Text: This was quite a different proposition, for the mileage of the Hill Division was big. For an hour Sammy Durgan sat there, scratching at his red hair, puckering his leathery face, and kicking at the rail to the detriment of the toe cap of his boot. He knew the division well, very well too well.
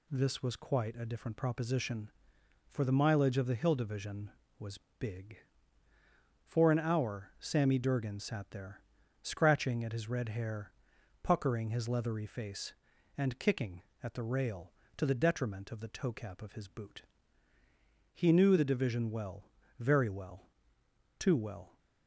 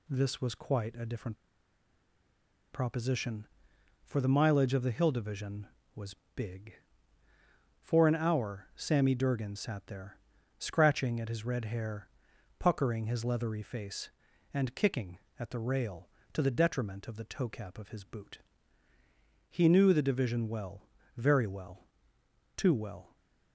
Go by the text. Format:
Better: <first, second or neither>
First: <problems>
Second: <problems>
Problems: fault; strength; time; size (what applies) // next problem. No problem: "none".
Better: first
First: pauses between "was" and "big"; slight; at 4.7 s; 0.22 s long // pauses between "well" and "too"; noticeable; at 20.4 s; 0.76 s long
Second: pauses between "different" and "proposition"; strong; at 1.3 s; 1.3 s long // pauses between "was" and "big"; slight; at 6.1 s; 0.22 s long // pauses between "well" and "too"; noticeable; at 21.7 s; 0.76 s long